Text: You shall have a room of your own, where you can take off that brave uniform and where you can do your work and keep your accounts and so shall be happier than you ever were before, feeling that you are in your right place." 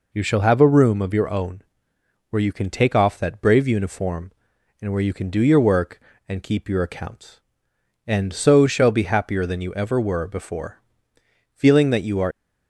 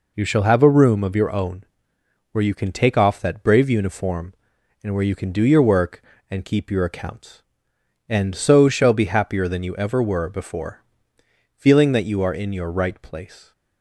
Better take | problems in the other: second | stops before "in your right place"; at 12.3 s

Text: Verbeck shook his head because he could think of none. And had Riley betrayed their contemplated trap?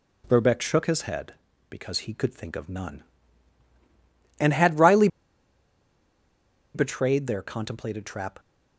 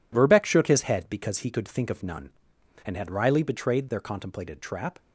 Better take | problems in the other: second | pauses between "Riley" and "betrayed"; strong; at 5.0 s; 1.6 s long

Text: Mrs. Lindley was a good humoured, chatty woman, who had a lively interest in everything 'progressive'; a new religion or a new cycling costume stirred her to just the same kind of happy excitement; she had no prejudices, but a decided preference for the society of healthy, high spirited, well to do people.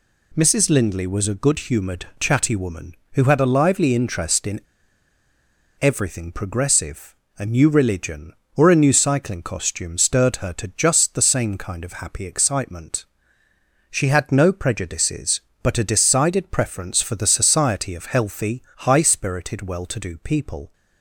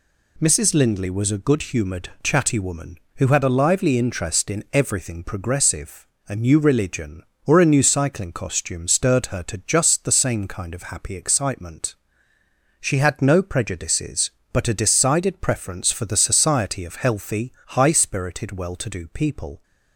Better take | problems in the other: second | pauses between "in" and "everything"; at 4.6 s; 1.1 s long

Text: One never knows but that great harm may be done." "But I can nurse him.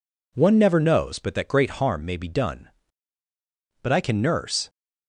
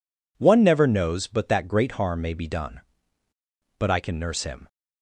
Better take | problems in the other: second | stops before "him"; at 4.6 s

